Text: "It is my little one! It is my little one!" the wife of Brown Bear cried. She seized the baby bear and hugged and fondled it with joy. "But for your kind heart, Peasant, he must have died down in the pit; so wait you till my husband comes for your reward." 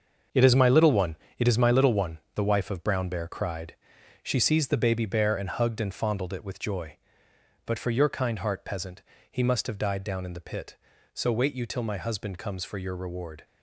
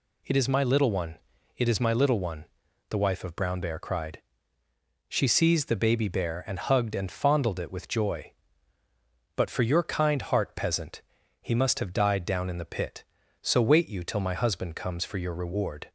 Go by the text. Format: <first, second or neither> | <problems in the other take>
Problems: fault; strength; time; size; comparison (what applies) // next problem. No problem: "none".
second | gets quieter; strong; throughout; 9 dB